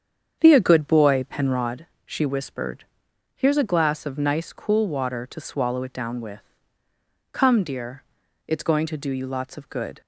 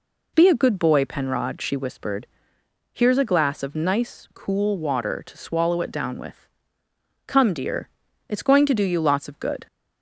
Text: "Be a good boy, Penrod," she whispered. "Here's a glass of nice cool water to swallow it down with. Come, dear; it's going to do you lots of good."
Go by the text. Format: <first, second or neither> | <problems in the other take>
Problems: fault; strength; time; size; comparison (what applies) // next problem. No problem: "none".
second | starts louder than the rest; strong; until 1.8 s; 8 dB